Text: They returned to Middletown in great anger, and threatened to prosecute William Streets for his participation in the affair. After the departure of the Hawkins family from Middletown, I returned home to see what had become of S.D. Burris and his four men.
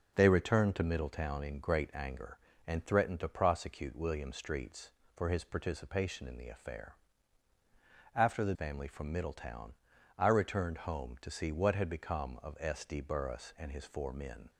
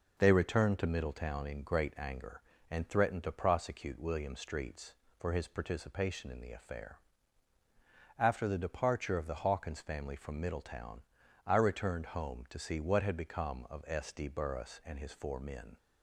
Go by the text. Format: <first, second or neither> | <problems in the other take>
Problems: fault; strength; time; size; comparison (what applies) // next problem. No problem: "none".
second | skips "departure of the Hawkins"; at 8.5 s